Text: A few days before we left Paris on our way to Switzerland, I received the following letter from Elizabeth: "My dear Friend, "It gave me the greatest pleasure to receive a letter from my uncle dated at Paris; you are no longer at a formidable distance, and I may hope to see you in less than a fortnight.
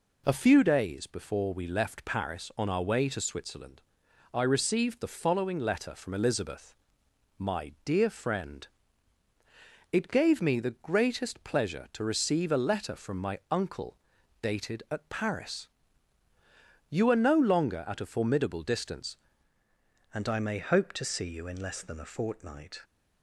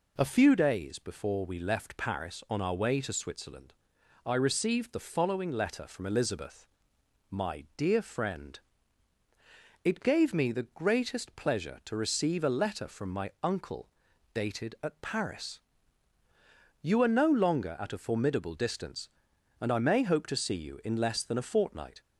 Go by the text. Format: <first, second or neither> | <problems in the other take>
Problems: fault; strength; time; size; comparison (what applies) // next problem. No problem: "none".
second | pauses between "uncle" and "dated"; at 13.9 s; 0.42 s long; also in the second // changes voice at "and"; from 20.1 s on; 2.7 s long